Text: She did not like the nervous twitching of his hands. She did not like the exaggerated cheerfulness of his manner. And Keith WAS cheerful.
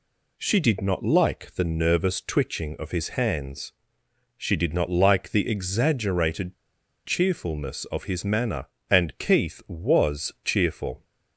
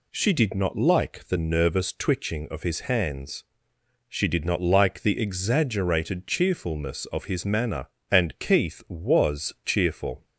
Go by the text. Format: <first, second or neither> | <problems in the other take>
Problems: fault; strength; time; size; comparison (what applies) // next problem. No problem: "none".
second | pauses between "exaggerated" and "cheerfulness"; noticeable; at 6.5 s; 0.51 s long